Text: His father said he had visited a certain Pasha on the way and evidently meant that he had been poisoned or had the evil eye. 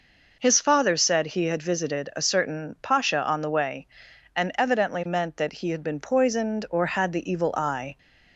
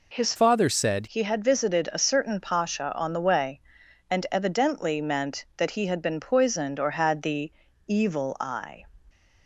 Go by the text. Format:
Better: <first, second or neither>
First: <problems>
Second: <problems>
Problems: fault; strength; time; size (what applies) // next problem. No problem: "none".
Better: first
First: none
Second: changes voice from "father" to "said"; from 0.3 to 1.0 s; 0.7 s long // pauses between "the" and "evil"; slight; at 7.5 s; 0.34 s long